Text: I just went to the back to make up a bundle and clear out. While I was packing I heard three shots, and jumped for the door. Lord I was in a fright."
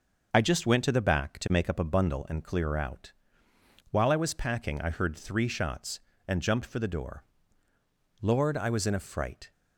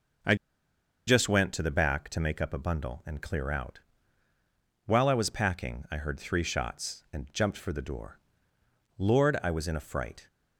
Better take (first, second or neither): first